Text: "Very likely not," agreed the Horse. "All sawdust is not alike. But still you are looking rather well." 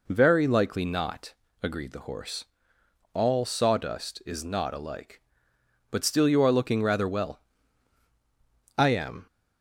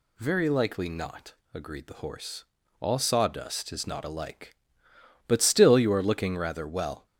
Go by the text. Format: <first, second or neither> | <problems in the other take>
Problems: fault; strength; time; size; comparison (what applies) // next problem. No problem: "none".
second | goes on to say "I am"; slight; from 8.7 s on; 0.48 s long